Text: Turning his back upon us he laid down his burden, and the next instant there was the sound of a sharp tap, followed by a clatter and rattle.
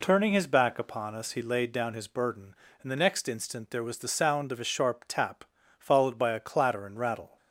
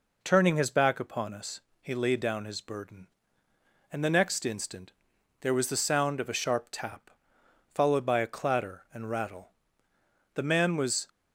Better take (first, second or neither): first